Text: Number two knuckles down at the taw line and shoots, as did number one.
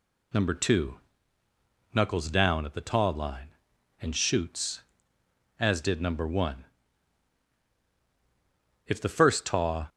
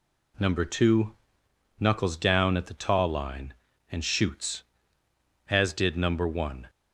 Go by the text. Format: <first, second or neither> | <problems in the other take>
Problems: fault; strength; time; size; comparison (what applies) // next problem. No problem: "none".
second | pauses between "two" and "knuckles"; noticeable; at 0.9 s; 0.98 s long; noticeable in the second // goes on to say "If the first taw"; noticeable; from 8.8 s on; 1.0 s long